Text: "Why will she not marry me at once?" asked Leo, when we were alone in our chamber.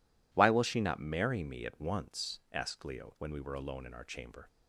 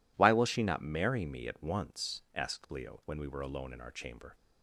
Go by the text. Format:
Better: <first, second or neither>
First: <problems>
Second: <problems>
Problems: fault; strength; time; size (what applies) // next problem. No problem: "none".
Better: neither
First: none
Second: none